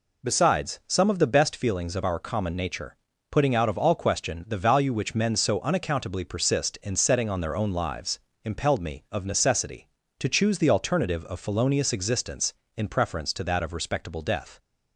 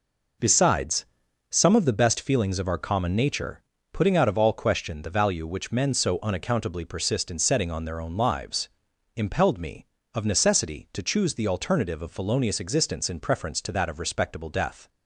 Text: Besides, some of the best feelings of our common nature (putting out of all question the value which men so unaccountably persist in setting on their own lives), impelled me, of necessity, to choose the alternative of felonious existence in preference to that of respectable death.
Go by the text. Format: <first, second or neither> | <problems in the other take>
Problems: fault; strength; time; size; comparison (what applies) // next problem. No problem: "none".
neither | none